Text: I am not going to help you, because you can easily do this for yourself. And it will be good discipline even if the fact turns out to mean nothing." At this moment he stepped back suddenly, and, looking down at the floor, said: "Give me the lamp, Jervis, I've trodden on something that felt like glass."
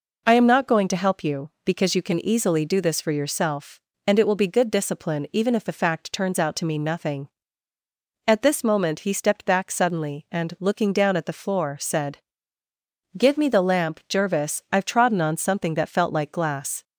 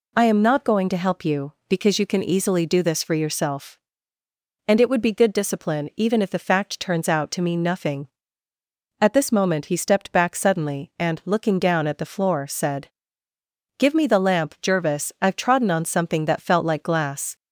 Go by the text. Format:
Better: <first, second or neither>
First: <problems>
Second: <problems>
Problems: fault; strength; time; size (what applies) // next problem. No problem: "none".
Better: first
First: none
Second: says "would" for "will"; at 4.8 s